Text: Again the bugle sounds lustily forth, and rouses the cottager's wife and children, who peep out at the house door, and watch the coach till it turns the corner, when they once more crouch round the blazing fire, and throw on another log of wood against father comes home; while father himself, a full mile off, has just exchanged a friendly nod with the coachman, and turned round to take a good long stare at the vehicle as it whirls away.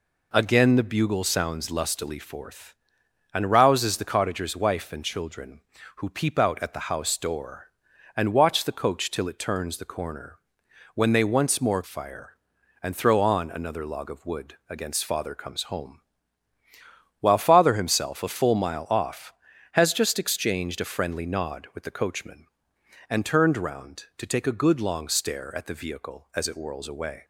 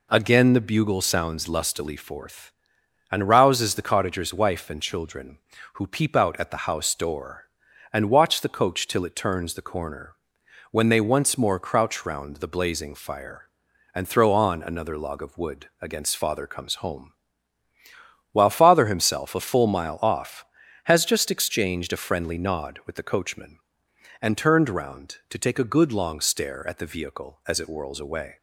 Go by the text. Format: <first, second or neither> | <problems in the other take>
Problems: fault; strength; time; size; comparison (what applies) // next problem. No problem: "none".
second | skips "crouch round the blazing"; at 11.8 s